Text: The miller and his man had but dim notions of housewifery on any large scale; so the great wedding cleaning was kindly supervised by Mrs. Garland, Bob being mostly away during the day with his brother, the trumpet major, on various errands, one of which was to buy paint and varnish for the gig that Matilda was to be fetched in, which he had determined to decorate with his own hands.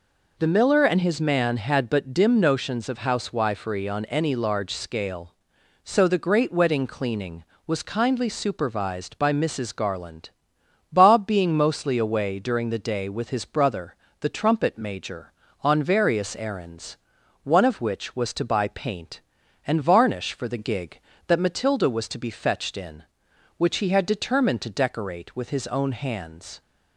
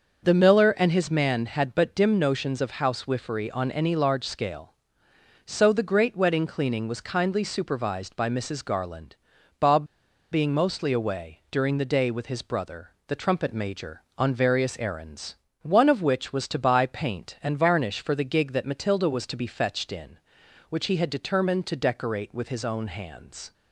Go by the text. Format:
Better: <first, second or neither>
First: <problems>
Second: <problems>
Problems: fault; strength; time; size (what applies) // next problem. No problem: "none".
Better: first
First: none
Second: starts louder than the rest; until 1.2 s; 6.5 dB // pauses between "Bob" and "being"; noticeable; at 9.8 s; 0.47 s long